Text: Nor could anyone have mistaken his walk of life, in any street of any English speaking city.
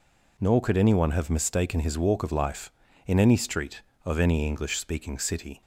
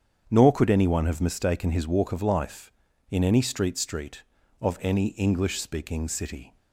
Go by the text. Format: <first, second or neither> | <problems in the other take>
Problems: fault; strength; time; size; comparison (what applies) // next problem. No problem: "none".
first | starts louder than the rest; strong; until 1.3 s; 8 dB // says "street" twice; at 3.7 s